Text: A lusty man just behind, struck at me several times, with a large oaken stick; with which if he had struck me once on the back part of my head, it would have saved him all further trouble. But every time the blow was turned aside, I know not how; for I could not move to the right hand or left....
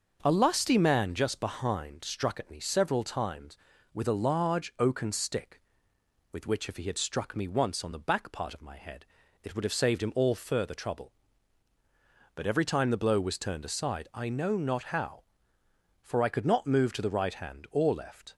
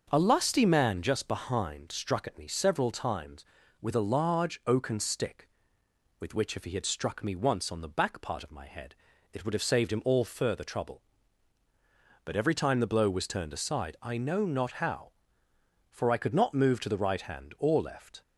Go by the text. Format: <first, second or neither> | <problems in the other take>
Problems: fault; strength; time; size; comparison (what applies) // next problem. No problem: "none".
neither | starts louder than the rest; the same in both